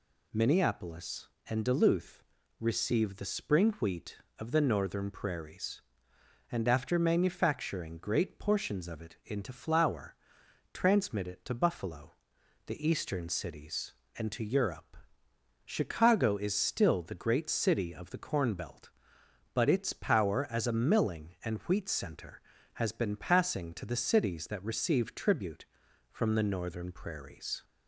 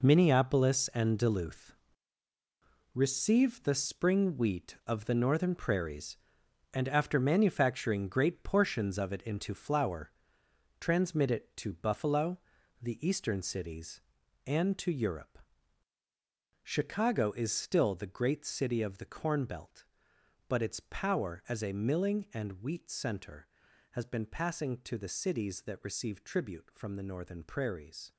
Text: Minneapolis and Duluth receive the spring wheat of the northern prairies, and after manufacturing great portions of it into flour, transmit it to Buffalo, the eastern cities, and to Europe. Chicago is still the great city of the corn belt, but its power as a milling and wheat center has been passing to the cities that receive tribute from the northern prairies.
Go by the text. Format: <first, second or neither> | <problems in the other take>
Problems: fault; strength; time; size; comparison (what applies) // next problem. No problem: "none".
first | gets quieter; strong; throughout; 10 dB // pauses between "Duluth" and "receive"; at 1.7 s; 1.2 s long; slight in the first